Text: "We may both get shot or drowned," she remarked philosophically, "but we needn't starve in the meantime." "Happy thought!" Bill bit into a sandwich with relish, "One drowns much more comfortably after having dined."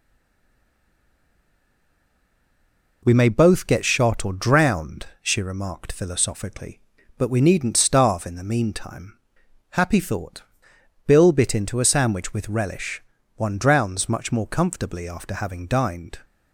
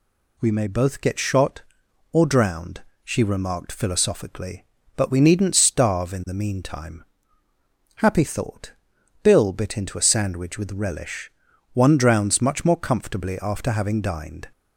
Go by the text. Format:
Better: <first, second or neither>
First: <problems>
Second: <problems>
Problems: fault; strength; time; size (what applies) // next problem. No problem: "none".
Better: second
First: stays silent before the first word; strong; until 3.0 s; 3.0 s long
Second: none